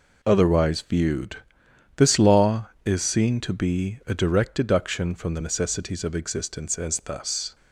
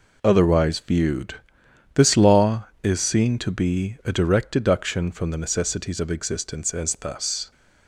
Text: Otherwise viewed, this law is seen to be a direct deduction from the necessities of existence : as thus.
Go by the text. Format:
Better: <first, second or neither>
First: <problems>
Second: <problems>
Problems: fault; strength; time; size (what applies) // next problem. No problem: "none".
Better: neither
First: none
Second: none